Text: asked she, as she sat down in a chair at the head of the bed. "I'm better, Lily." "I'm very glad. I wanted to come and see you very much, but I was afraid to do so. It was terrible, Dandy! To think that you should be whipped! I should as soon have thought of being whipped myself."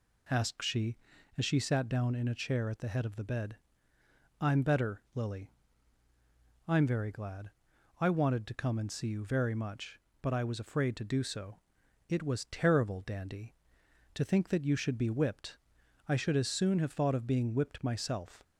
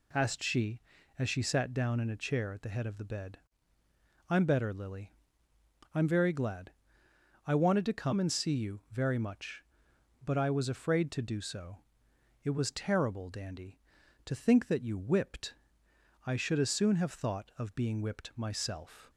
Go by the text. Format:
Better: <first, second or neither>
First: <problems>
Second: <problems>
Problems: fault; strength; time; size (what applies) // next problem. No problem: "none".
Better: first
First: none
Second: skips "should be"; at 14.9 s